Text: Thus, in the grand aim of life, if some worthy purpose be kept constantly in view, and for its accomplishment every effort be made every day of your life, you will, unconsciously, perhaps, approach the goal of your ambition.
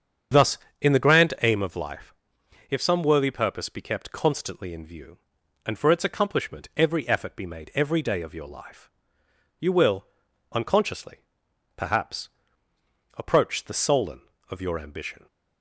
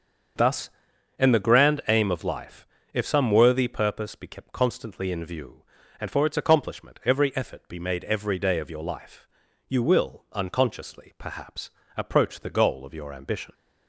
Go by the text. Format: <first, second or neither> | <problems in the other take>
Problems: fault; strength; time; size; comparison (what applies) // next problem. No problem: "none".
second | starts louder than the rest; strong; until 1.6 s; 7.5 dB; also in the second // says "solen" for "goal"; at 13.7 s